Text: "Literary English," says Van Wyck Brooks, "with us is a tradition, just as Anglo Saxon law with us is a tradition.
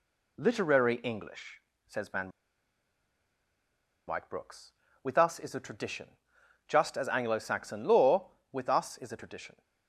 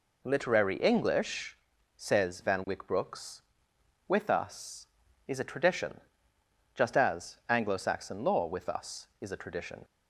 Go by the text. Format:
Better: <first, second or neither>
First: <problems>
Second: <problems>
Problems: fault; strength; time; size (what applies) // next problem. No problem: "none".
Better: second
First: pauses between "Van" and "Wyck"; strong; at 2.3 s; 1.7 s long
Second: none